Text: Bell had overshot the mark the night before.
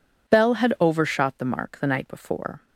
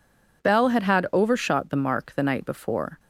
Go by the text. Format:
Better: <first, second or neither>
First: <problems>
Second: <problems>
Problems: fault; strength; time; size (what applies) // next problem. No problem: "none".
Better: first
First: none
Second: says "had" twice; at 0.8 s